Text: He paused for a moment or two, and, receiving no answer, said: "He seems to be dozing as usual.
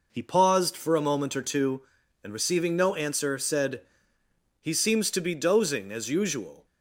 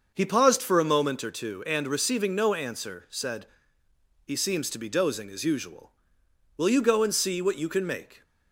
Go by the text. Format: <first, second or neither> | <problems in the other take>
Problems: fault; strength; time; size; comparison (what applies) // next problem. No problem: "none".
first | starts louder than the rest; until 1.1 s; 6.5 dB // goes on to say "Will you go and see what you can make"; from 6.5 s on; 1.6 s long